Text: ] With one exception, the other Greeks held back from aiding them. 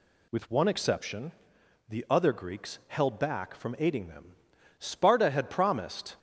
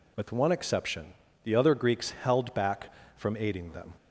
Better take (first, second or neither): second